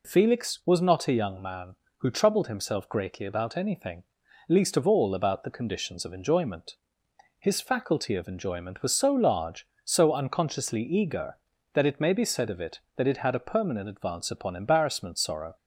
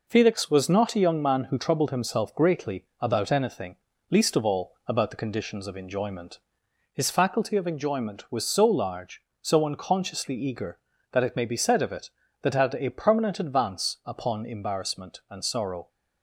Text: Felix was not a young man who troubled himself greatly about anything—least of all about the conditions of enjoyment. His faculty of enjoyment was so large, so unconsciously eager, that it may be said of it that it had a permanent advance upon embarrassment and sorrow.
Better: second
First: skips "and"; at 15.1 s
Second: none

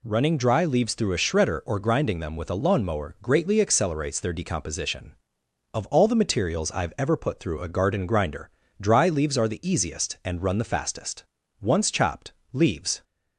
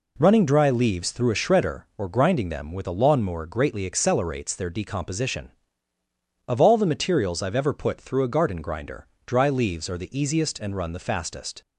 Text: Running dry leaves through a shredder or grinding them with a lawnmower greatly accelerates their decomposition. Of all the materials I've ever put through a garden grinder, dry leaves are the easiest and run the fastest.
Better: second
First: goes on to say "Once chopped leaves"; from 11.6 s on; 1.4 s long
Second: none

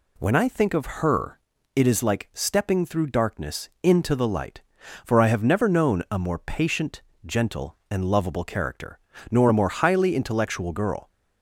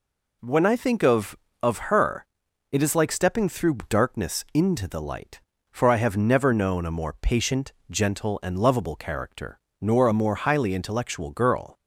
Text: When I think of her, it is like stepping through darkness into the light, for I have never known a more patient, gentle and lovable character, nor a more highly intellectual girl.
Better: first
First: none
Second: says "of" twice; at 1.6 s

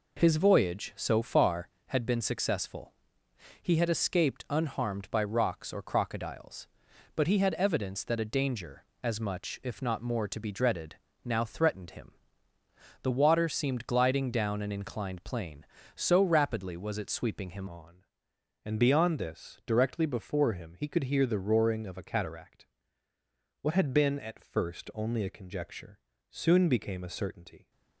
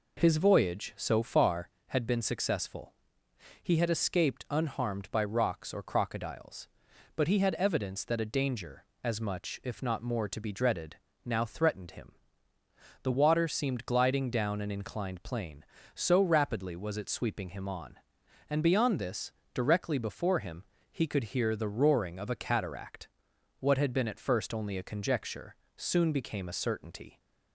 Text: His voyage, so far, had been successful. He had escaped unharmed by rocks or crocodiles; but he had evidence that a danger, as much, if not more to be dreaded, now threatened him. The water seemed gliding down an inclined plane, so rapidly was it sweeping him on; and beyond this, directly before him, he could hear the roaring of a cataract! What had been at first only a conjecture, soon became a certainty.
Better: second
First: changes voice at "on"; from 17.6 s on; 10.1 s long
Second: none

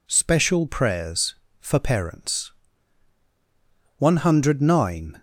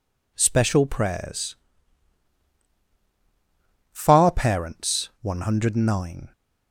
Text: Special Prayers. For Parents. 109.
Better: first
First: none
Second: says "Far" for "For"; at 3.9 s

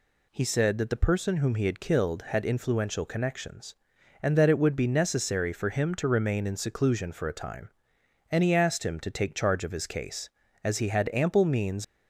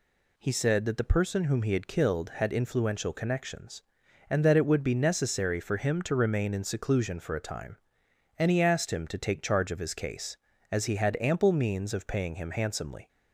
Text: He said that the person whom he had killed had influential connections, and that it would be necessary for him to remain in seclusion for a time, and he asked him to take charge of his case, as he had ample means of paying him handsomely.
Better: second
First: stops before "of paying him handsomely"; at 11.8 s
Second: none

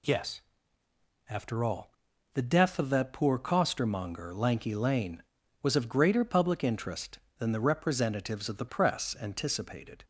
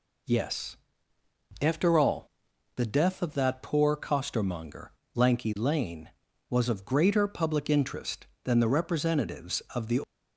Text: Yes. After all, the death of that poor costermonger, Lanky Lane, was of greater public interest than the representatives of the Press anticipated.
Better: first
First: none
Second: stops before "Press anticipated"; at 10.0 s

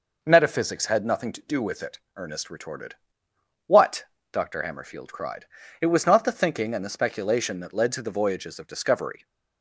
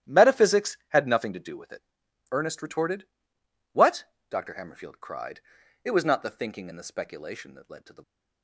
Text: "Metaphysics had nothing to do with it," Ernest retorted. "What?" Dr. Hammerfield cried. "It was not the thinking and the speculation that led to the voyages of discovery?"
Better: first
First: none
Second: starts louder than the rest; strong; until 1.2 s; 12 dB // stops before "voyages of discovery"; at 8.0 s

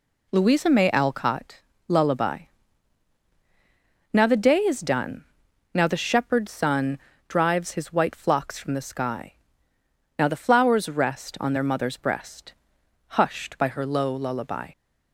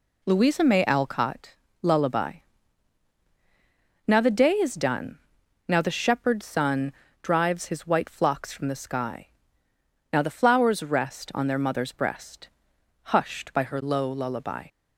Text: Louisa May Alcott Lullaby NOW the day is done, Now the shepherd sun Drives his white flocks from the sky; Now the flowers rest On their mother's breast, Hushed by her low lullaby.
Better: neither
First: pauses between "Alcott" and "Lullaby"; slight; at 1.6 s; 0.26 s long // pauses between "Lullaby" and "NOW"; strong; at 2.3 s; 1.7 s long // pauses between "sun" and "Drives"; slight; at 6.9 s; 0.30 s long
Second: pauses between "Alcott" and "Lullaby"; slight; at 1.5 s; 0.26 s long // pauses between "Lullaby" and "NOW"; strong; at 2.3 s; 1.7 s long // pauses between "sun" and "Drives"; slight; at 6.9 s; 0.30 s long

